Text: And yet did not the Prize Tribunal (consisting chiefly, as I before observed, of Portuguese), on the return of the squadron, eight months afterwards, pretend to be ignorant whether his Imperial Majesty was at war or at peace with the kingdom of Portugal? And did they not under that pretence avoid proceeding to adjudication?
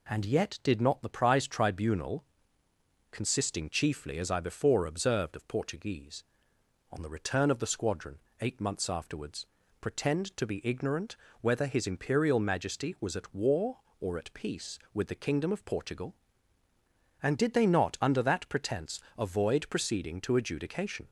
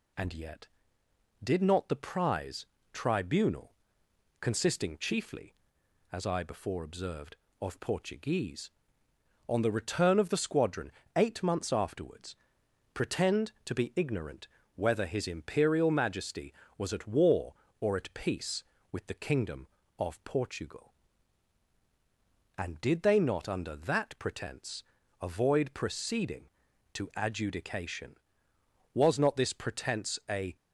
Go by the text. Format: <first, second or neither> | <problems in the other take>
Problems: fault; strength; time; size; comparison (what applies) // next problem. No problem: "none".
first | pauses between "Prize" and "Tribunal"; slight; at 2.6 s; 0.26 s long // pauses between "ignorant" and "whether"; slight; at 14.4 s; 0.28 s long; slight in the first // pauses between "pretence" and "avoid"; slight; at 24.8 s; 0.36 s long; slight in the first // goes on to say "Was not this pretence a"; from 28.9 s on; 1.6 s long